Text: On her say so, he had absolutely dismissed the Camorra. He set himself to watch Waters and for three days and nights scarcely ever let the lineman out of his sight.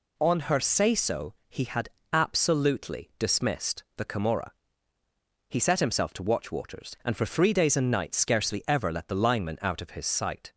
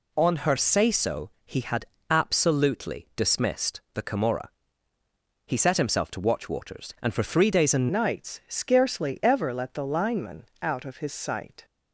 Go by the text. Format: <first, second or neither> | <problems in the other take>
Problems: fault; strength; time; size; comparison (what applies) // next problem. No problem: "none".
first | pauses between "had" and "absolutely"; slight; at 1.8 s; 0.24 s long; slight in the first // changes voice at "nights"; from 7.9 s on; 3.7 s long // pauses between "lineman" and "out"; slight; at 10.4 s; 0.18 s long